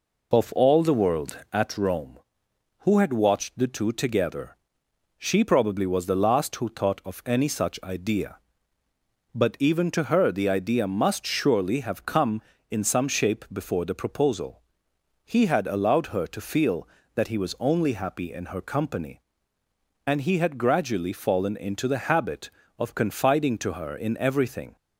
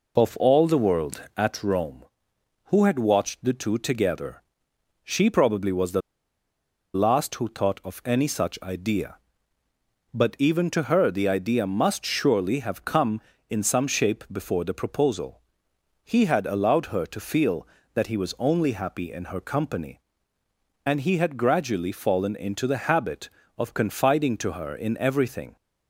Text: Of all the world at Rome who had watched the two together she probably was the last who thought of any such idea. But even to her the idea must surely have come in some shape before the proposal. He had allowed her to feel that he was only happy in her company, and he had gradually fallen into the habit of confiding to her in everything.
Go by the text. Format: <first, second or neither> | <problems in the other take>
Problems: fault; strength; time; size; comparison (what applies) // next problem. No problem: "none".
first | pauses between "together" and "she"; noticeable; at 4.4 s; 0.64 s long; noticeable in the first // pauses between "the" and "last"; noticeable; at 6.0 s; 0.93 s long